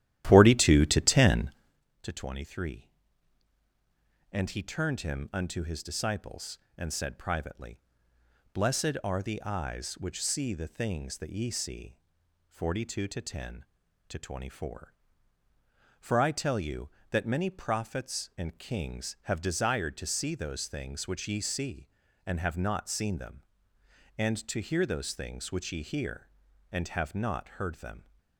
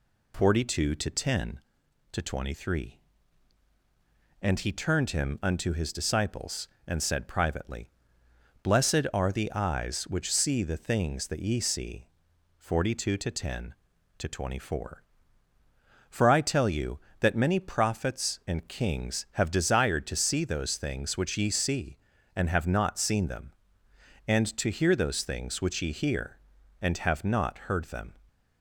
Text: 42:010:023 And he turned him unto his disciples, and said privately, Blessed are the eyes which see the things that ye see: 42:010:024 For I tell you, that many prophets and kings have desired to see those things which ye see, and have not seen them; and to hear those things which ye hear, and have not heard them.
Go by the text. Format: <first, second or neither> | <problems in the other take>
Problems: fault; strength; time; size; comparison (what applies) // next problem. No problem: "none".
second | starts louder than the rest; strong; until 1.9 s; 13 dB